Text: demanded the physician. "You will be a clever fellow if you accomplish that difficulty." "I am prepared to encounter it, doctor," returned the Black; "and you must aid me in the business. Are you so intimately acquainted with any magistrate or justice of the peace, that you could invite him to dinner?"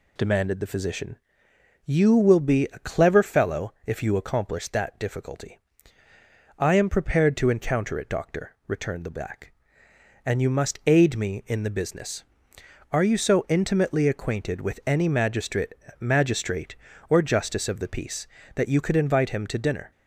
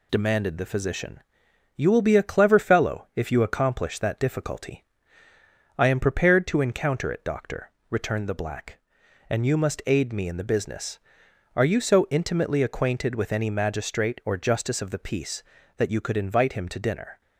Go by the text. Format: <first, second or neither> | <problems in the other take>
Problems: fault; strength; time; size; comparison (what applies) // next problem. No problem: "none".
second | says "magistrate" twice; at 15.9 s